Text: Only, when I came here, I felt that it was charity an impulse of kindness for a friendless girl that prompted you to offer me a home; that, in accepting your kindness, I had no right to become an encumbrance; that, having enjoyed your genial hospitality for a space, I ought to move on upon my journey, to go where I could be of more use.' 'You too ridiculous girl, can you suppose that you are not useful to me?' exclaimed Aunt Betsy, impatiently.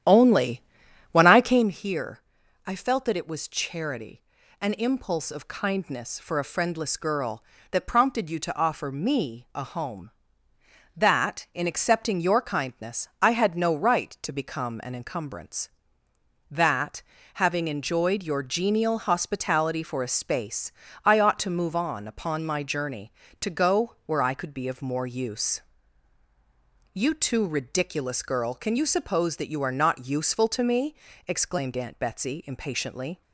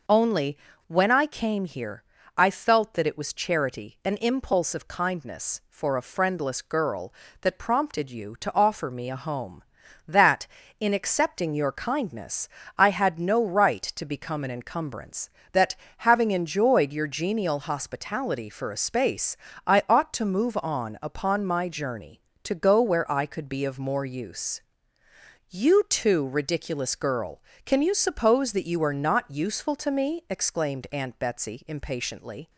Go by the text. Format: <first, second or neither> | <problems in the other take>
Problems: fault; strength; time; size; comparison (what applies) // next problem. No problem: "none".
second | starts louder than the rest; strong; until 1.7 s; 10.5 dB // pauses between "charity" and "an"; at 4.2 s; 0.40 s long